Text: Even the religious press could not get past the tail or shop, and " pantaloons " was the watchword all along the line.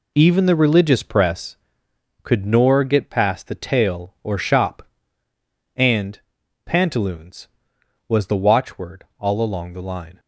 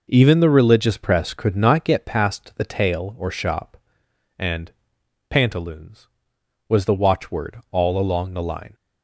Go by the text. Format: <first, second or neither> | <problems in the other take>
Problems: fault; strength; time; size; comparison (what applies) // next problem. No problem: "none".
second | says "nor" for "not"; at 2.4 s